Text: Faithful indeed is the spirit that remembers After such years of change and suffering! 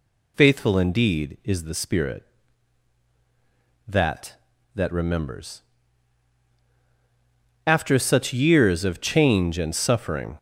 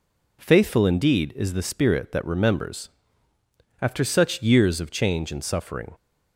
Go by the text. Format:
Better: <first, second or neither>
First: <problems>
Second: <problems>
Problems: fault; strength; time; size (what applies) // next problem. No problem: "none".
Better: second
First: says "that" twice; at 4.7 s // pauses between "remembers" and "After"; strong; at 5.6 s; 2.0 s long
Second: pauses between "remembers" and "After"; noticeable; at 2.8 s; 0.94 s long